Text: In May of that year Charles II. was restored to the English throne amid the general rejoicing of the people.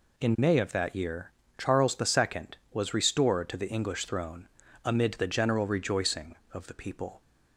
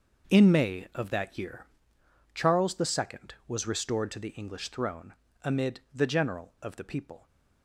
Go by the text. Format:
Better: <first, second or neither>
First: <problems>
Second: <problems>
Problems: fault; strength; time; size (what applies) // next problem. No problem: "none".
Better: first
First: pauses between "year" and "Charles"; slight; at 1.3 s; 0.26 s long // pauses between "throne" and "amid"; slight; at 4.4 s; 0.34 s long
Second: starts louder than the rest; noticeable; until 1.3 s; 6 dB // pauses between "year" and "Charles"; noticeable; at 1.6 s; 0.66 s long // pauses between "throne" and "amid"; slight; at 5.1 s; 0.30 s long // skips "rejoicing"; at 6.5 s